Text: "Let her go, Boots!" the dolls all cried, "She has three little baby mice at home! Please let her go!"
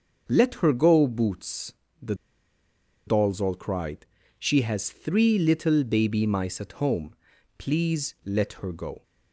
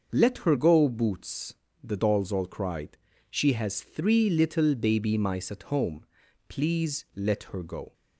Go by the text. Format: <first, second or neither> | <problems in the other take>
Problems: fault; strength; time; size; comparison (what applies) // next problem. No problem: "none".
second | starts louder than the rest; until 1.2 s; 6.5 dB; also in the second // pauses between "the" and "dolls"; noticeable; at 2.1 s; 0.92 s long